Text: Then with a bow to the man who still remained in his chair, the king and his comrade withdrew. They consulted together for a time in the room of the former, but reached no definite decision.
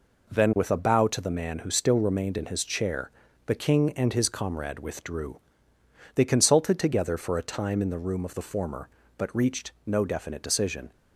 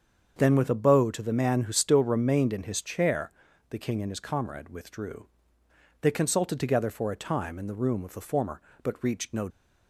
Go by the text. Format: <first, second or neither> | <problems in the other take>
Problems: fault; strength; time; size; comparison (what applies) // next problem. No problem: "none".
first | starts louder than the rest; until 1.4 s; 7 dB // stops before "definite decision"; at 9.5 s